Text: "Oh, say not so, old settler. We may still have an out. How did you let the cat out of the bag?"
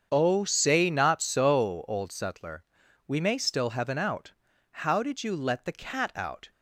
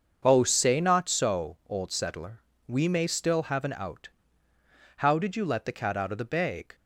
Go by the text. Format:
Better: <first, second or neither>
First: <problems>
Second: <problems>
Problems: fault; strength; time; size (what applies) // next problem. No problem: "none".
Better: second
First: starts louder than the rest; strong; until 1.1 s; 7.5 dB // stops before "of the bag"; at 6.5 s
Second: starts louder than the rest; until 1.2 s; 6.5 dB